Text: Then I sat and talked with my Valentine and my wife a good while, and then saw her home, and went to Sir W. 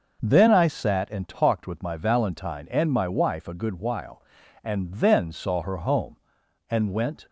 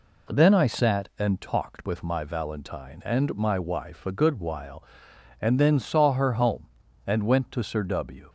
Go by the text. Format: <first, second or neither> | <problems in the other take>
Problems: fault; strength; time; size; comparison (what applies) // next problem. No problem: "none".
second | starts louder than the rest; noticeable; until 1.2 s; 6 dB // stops before "to Sir W"; at 7.2 s